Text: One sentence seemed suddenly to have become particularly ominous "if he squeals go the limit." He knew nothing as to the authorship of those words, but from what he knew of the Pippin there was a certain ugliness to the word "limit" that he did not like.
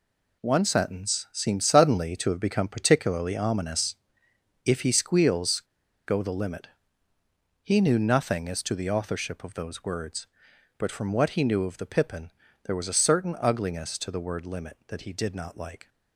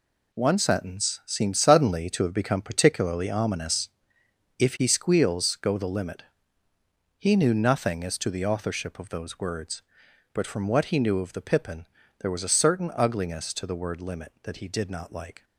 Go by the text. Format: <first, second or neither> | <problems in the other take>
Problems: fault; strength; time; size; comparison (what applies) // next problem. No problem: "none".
second | pauses between "ominous" and "if"; noticeable; at 3.9 s; 0.68 s long; noticeable in the second // pauses between "squeals" and "go"; noticeable; at 5.5 s; 0.48 s long // pauses between "Pippin" and "there"; slight; at 12.3 s; 0.34 s long; slight in the second